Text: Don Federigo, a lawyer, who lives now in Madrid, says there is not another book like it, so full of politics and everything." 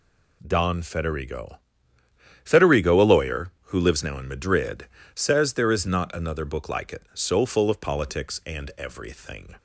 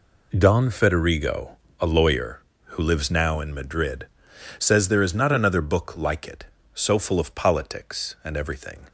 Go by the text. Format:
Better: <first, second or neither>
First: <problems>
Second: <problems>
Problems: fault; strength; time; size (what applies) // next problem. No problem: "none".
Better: second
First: says "Federigo" twice; at 2.4 s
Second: none